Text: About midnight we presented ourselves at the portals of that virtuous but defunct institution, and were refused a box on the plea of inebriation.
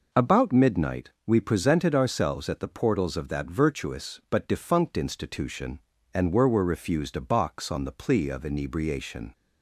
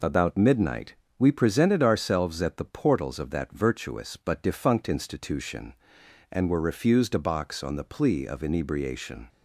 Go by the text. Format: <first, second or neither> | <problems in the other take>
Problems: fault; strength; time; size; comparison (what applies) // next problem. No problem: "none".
second | pauses between "midnight" and "we"; slight; at 1.0 s; 0.18 s long; slight in the second // says "were" twice; at 6.4 s